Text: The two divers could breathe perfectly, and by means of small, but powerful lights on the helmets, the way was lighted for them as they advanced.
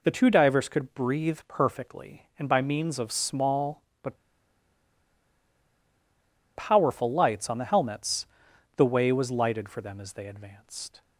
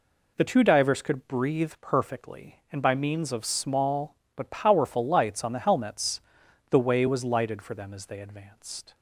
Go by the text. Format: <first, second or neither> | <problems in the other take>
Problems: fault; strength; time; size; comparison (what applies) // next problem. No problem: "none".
second | pauses between "but" and "powerful"; strong; at 4.1 s; 2.3 s long